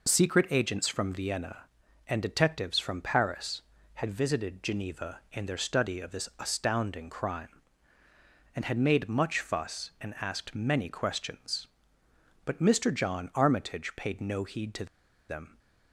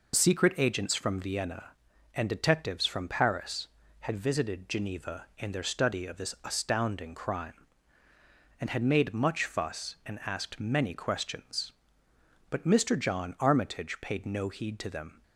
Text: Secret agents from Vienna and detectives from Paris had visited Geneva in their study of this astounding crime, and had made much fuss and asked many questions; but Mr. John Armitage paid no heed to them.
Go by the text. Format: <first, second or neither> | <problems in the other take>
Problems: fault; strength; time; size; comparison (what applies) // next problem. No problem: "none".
second | pauses between "to" and "them"; at 14.8 s; 0.43 s long